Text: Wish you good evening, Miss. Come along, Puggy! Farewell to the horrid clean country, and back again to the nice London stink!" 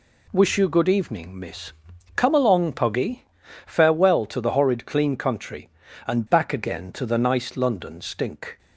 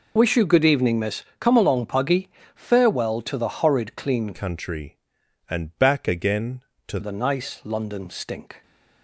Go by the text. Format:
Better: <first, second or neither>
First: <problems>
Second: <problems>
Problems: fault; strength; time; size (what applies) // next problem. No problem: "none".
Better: first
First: none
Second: changes voice from "country" to "to"; from 4.3 to 6.9 s; 2.6 s long